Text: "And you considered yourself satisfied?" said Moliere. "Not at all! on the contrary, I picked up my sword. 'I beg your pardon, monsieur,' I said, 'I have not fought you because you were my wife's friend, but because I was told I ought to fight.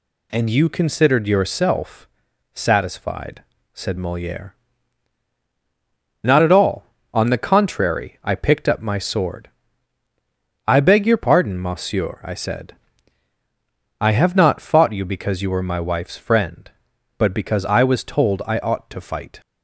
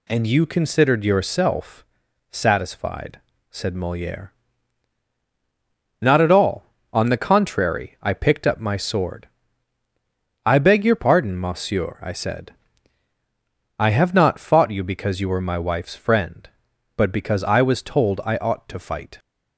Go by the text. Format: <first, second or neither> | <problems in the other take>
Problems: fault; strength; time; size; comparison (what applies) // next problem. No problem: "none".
neither | pauses between "yourself" and "satisfied"; noticeable; the same in both